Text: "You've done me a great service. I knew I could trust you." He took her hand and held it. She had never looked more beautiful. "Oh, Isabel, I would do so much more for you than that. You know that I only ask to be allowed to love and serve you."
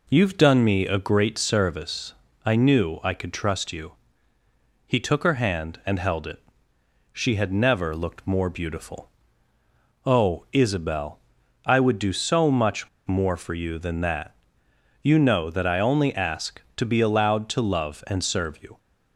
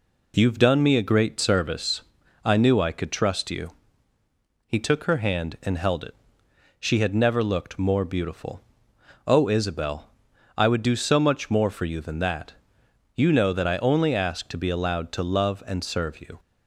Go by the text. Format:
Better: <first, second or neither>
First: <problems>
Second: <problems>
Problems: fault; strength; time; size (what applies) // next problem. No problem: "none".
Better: second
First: pauses between "much" and "more"; slight; at 12.8 s; 0.18 s long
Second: none